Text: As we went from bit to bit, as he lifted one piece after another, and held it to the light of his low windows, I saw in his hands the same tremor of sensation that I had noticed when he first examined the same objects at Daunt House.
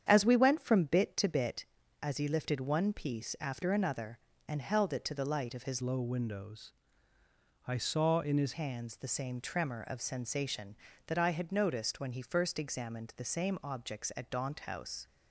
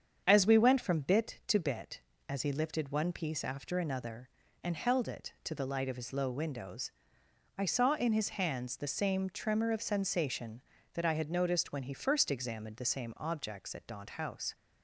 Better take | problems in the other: second | starts louder than the rest; strong; until 1.0 s; 8.5 dB; strong in the second // changes voice from "low" to "his"; from 5.8 to 8.5 s; 2.7 s long

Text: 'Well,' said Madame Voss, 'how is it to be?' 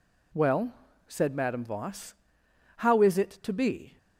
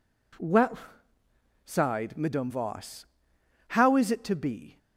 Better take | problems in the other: first | says "sighed" for "said"; at 1.6 s

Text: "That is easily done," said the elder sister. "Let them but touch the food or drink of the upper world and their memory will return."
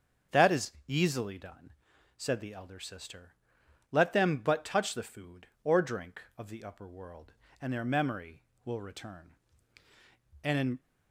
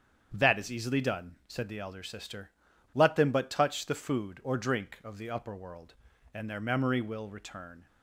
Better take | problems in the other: second | starts louder than the rest; strong; until 1.4 s; 7 dB; strong in the second // pauses between "is" and "easily"; slight; at 0.7 s; 0.16 s long // goes on to say "And in"; slight; from 10.4 s on; 0.36 s long

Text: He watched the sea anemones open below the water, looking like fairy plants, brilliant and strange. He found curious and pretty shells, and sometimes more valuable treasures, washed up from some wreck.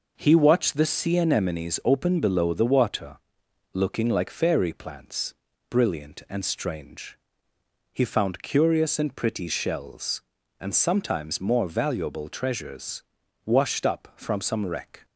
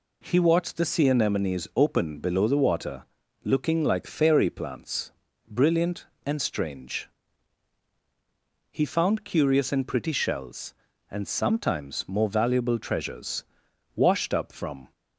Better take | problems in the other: first | stops before "some wreck"; at 14.9 s

